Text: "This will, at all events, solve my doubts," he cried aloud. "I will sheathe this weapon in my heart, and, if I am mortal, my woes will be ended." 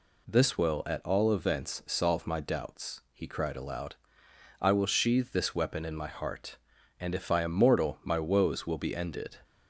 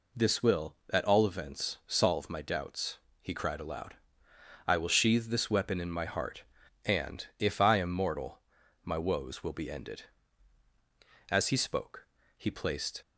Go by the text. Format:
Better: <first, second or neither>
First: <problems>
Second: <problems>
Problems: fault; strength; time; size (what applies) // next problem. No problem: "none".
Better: first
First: none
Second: goes on to say "As he spoke he placed"; strong; from 11.3 s on; 1.7 s long